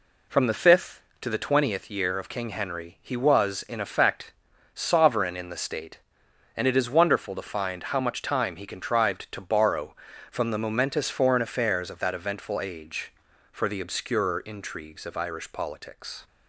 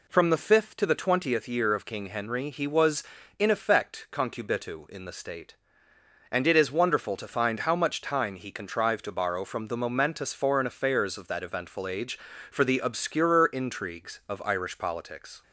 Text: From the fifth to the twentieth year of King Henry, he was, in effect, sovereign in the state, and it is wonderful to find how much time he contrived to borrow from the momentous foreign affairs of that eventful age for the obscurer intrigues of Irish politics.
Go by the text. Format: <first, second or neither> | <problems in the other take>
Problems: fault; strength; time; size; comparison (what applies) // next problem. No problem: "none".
first | says "concubitu" for "sovereign"; at 4.1 s